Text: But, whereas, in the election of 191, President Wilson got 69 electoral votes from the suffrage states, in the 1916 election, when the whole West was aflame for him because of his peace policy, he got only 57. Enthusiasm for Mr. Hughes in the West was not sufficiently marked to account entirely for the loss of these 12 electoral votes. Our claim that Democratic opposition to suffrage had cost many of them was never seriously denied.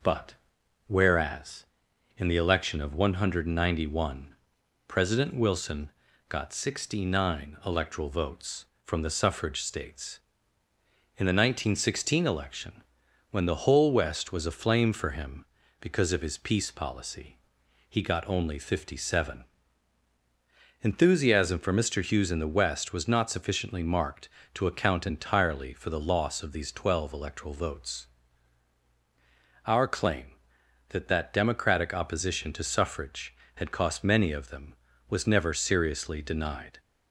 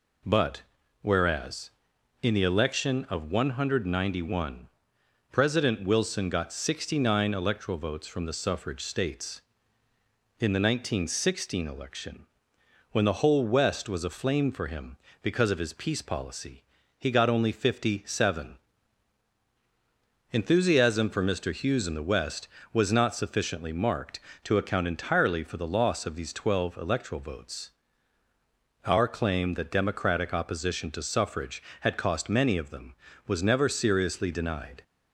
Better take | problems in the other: second | pauses between "Wilson" and "got"; at 5.8 s; 0.38 s long // says "that" twice; at 31.0 s

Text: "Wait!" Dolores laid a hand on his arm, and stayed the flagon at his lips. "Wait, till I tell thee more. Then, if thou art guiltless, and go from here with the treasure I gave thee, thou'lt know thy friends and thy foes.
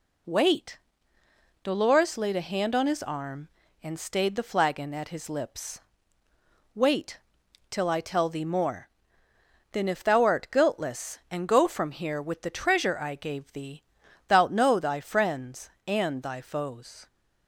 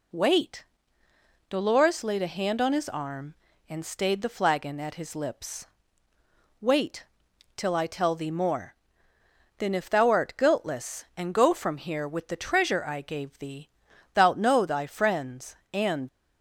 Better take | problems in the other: first | stops before "thy foes"; at 16.0 s

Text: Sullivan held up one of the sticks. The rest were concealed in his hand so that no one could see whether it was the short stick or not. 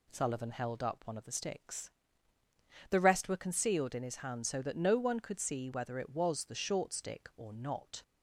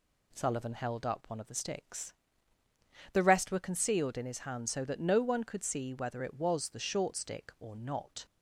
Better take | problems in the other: neither | none

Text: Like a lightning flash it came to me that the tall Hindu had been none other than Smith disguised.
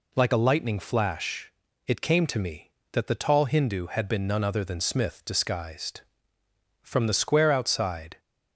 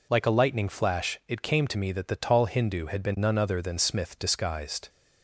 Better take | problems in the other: second | pauses between "flash" and "it"; slight; at 1.5 s; 0.34 s long // goes on to say "From the square outside"; from 6.8 s on; 1.3 s long

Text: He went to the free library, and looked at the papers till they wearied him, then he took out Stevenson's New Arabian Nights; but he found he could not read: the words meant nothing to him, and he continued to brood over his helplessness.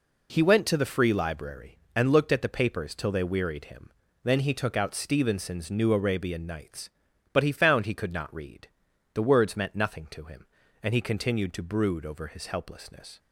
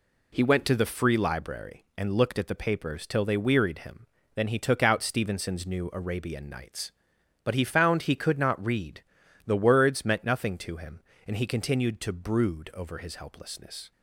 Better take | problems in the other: neither | none

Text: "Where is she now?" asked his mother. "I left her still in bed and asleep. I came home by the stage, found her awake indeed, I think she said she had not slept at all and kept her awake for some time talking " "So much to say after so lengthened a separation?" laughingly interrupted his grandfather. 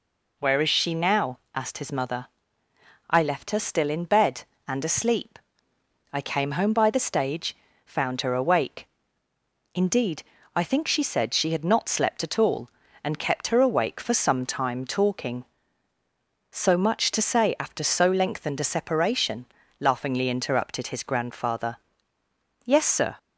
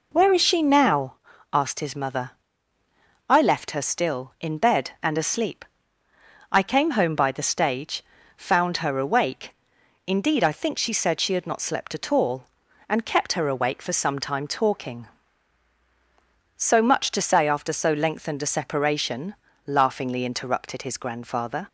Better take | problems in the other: second | pauses between "awake" and "indeed"; noticeable; at 8.8 s; 0.88 s long; noticeable in the second // goes on to say "Yes sir"; from 22.6 s on; 0.52 s long

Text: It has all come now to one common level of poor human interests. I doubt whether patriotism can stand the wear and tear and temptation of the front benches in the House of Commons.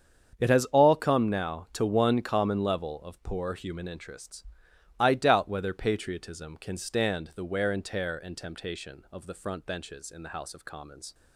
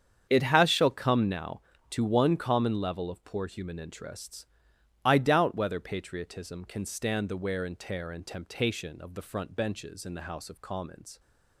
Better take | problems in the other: first | starts louder than the rest; strong; until 1.3 s; 8 dB; strong in the first // says "shall" for "all"; at 0.6 s

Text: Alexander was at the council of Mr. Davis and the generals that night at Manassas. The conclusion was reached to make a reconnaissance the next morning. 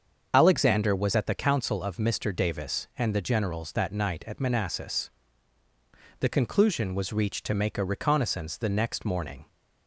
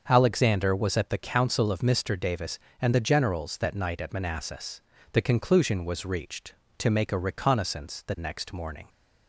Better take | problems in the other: second | loses the start of "Alexander"; at 0.3 s; 55 ms // starts louder than the rest; until 1.3 s; 7 dB; also in the second

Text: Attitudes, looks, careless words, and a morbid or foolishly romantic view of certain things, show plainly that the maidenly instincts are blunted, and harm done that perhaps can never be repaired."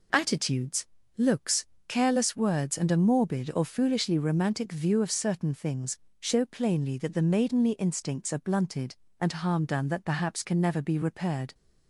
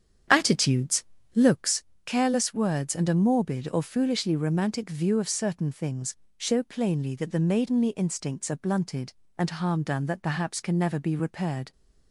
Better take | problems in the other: first | starts louder than the rest; strong; until 1.7 s; 8.5 dB

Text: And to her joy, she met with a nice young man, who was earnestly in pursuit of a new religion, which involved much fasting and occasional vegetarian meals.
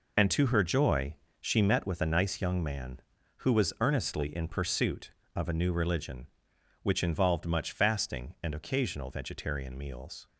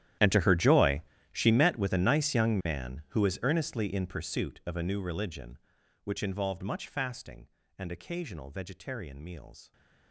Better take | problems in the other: first | gets quieter; strong; throughout; 20.5 dB

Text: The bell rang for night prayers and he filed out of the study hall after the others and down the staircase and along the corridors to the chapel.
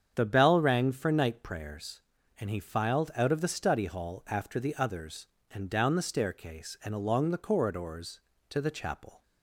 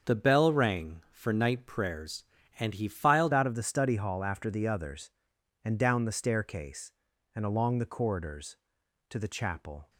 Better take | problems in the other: first | starts louder than the rest; until 1.1 s; 7 dB; strong in the first // changes voice at "out"; from 3.3 s on; 6.5 s long

